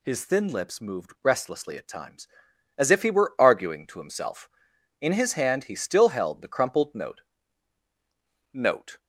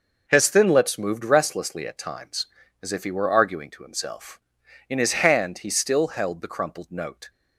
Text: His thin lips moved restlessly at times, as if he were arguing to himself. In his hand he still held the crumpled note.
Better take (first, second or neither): second